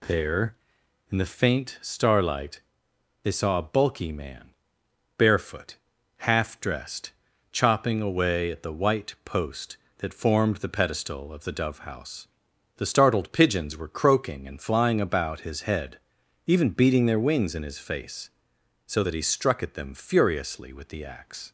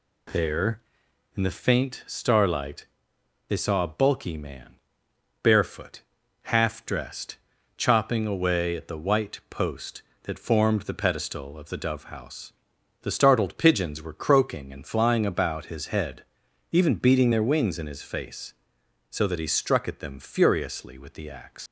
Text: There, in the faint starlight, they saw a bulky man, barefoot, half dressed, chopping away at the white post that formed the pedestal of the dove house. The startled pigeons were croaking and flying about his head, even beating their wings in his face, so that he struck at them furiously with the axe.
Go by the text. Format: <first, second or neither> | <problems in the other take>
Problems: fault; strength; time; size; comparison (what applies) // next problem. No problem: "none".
first | leaves "axe" unfinished; at 21.6 s; 105 ms